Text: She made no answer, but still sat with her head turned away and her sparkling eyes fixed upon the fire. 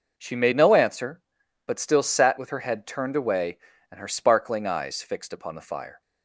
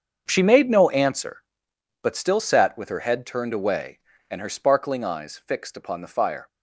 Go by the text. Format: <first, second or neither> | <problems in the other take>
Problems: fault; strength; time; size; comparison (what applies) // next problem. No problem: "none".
first | gets quieter; strong; throughout; 15 dB